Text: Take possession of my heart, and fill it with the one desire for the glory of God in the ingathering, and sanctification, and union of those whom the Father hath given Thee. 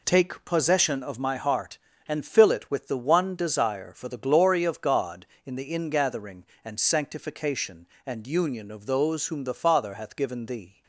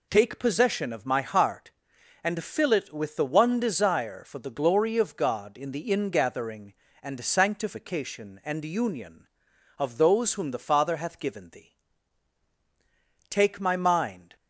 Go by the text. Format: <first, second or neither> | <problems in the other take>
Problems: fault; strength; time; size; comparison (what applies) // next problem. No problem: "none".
first | goes on to say "Take my mind"; noticeable; from 13.2 s on; 1.0 s long